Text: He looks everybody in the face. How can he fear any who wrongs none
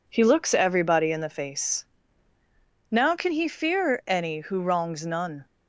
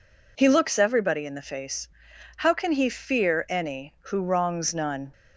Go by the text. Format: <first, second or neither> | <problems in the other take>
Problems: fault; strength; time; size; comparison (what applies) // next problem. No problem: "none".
second | says "Now" for "How"; at 2.9 s